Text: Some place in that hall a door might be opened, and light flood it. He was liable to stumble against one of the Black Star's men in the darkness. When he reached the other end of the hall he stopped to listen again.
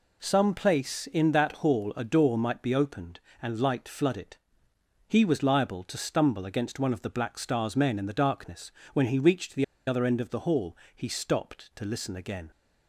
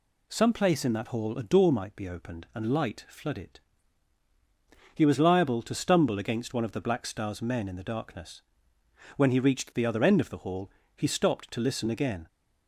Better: second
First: pauses between "the" and "other"; slight; at 9.6 s; 0.23 s long // pauses between "hall" and "he"; slight; at 10.7 s; 0.20 s long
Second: pauses between "hall" and "he"; slight; at 10.7 s; 0.26 s long

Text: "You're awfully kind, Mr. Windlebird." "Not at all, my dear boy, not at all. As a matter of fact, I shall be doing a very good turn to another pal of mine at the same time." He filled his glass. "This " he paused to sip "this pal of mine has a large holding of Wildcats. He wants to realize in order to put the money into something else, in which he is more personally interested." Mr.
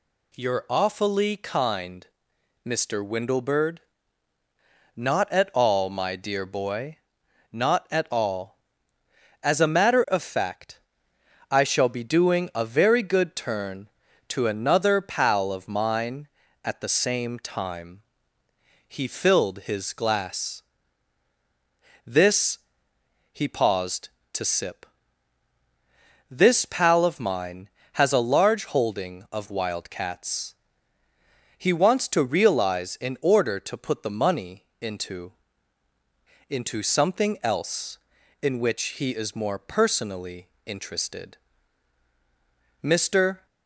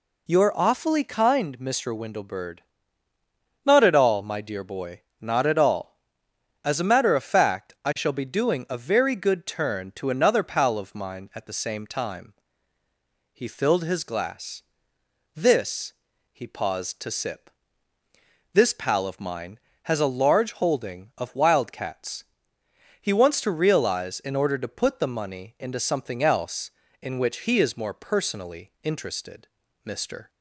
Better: second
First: pauses between "sip" and "this"; strong; at 24.8 s; 1.4 s long // says "into" twice; at 36.4 s // pauses between "which" and "he"; slight; at 38.8 s; 0.18 s long // pauses between "personally" and "interested"; slight; at 40.4 s; 0.18 s long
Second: pauses between "sip" and "this"; at 17.4 s; 1.0 s long

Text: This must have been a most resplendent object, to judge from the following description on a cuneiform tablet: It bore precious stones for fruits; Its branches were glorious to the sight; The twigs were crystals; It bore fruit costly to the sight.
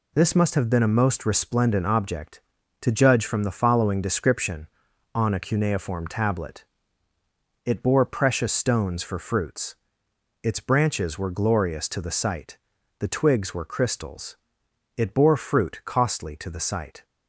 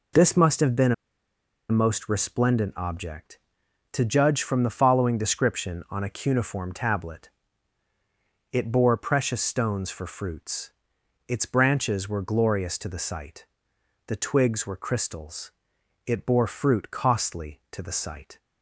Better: first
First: none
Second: pauses between "been" and "a"; noticeable; at 0.9 s; 0.77 s long

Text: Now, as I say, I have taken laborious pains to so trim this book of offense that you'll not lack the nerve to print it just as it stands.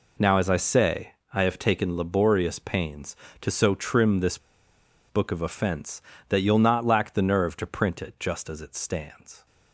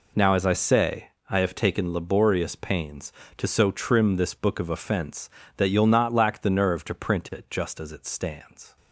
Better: second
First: pauses between "this" and "book"; noticeable; at 4.3 s; 0.70 s long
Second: none

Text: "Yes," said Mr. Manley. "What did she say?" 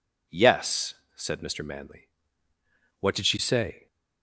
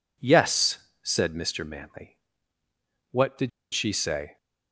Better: first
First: none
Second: pauses between "did" and "she"; slight; at 3.4 s; 0.24 s long

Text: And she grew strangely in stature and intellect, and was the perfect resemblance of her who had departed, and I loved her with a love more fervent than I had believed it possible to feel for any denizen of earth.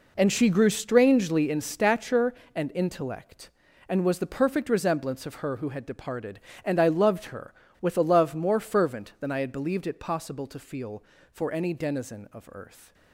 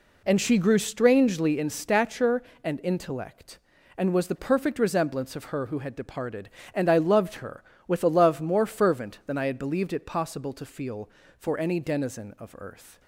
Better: second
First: gets quieter; strong; throughout; 12 dB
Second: none

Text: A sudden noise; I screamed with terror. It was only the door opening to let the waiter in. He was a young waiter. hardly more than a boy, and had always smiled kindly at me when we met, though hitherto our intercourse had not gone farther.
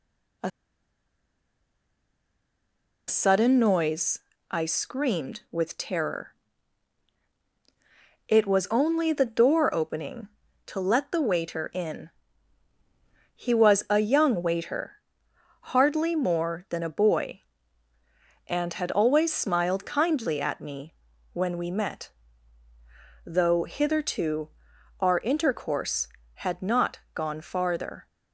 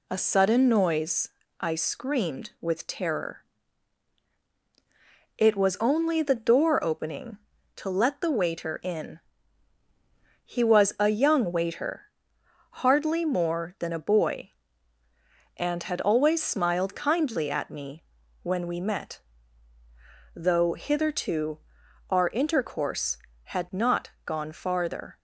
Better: second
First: pauses between "A" and "sudden"; strong; at 0.5 s; 2.5 s long // pauses between "me" and "when"; at 20.9 s; 0.38 s long // pauses between "hitherto" and "our"; noticeable; at 24.4 s; 0.52 s long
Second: pauses between "me" and "when"; at 18.0 s; 0.38 s long // pauses between "hitherto" and "our"; noticeable; at 21.5 s; 0.52 s long

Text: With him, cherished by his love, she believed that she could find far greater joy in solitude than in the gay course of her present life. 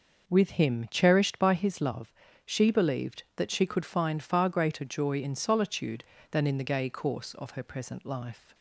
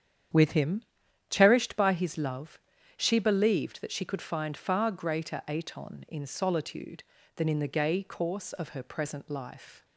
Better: first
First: none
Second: starts louder than the rest; strong; until 1.7 s; 9 dB // says "aton" for "joy"; at 5.4 s

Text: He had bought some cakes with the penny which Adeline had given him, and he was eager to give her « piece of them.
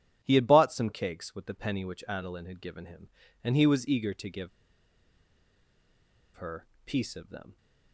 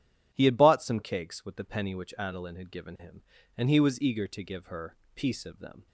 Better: second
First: pauses between "give" and "her"; strong; at 4.4 s; 1.8 s long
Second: none

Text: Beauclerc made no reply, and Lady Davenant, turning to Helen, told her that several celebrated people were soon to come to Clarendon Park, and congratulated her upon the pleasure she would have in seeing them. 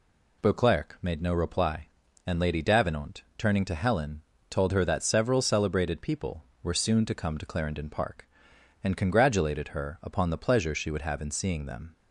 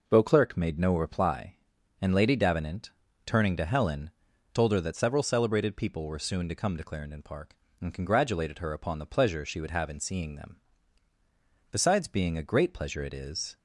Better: first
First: none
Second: goes on to say "Besides being a great pleasure it is"; strong; from 11.7 s on; 1.8 s long

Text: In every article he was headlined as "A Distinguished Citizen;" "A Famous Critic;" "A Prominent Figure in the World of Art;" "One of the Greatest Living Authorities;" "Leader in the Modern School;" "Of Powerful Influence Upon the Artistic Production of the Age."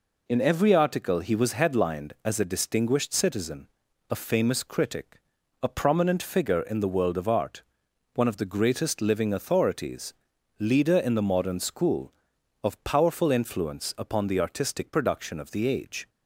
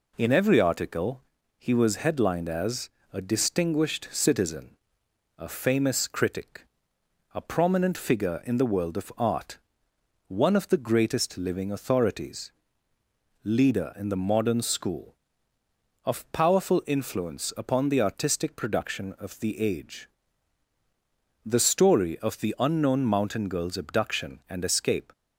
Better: first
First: none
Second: pauses between "article" and "he"; slight; at 1.2 s; 0.34 s long // pauses between "as" and "A"; slight; at 2.8 s; 0.24 s long // goes on to say "The story of the unknown mountain girl's abduction and escape"; strong; from 21.4 s on; 3.6 s long

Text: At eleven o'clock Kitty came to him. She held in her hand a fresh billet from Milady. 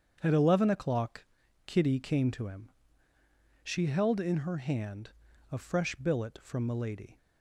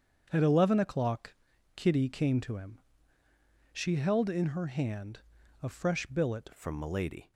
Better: first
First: starts louder than the rest; strong; until 1.2 s; 7.5 dB // pauses between "o'clock" and "Kitty"; at 1.2 s; 0.42 s long // pauses between "hand" and "a"; at 5.1 s; 0.40 s long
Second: starts louder than the rest; strong; until 1.3 s; 7.5 dB // pauses between "o'clock" and "Kitty"; at 1.3 s; 0.42 s long // pauses between "hand" and "a"; at 5.2 s; 0.42 s long // changes voice at "from"; from 6.5 s on; 0.8 s long

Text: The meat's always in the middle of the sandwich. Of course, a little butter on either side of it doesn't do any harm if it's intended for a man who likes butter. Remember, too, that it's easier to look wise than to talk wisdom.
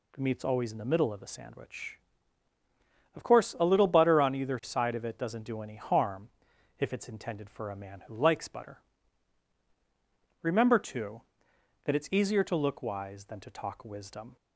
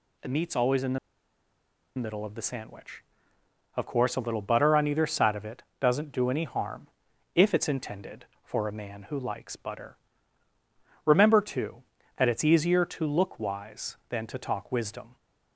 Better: first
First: pauses between "harm" and "if"; noticeable; at 6.2 s; 0.50 s long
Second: pauses between "the" and "middle"; at 0.9 s; 0.99 s long // pauses between "it" and "doesn't"; slight; at 5.6 s; 0.18 s long // pauses between "harm" and "if"; noticeable; at 6.8 s; 0.46 s long

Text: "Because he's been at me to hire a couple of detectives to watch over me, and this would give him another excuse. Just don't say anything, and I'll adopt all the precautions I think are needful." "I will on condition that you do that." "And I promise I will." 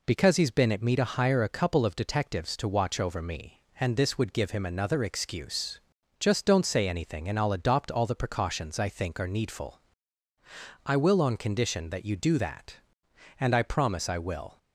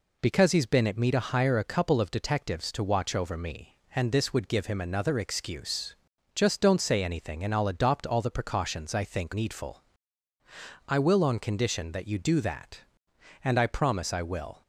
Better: first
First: none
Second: skips "are"; at 9.3 s

